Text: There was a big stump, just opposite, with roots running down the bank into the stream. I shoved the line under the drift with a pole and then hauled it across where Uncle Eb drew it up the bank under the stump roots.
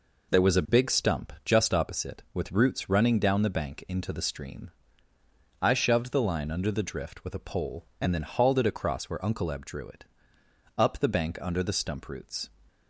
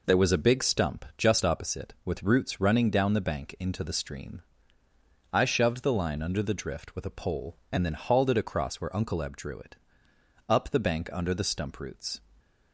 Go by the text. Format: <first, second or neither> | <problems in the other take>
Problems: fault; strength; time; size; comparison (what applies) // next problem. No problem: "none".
neither | pauses between "it" and "up"; noticeable; the same in both